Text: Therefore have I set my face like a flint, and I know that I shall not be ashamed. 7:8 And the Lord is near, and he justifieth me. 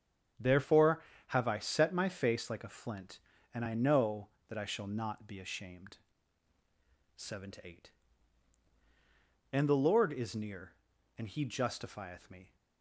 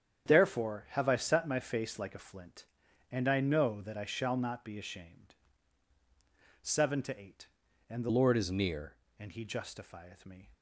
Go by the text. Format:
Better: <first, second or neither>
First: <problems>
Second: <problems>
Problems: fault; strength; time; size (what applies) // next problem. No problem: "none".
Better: first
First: starts louder than the rest; strong; until 1.6 s; 8 dB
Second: starts louder than the rest; strong; until 1.3 s; 8.5 dB // changes voice from "Lord" to "near"; from 8.0 to 8.9 s; 0.9 s long